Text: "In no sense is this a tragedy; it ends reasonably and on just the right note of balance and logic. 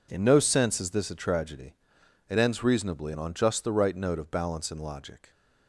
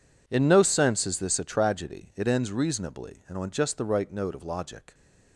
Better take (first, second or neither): first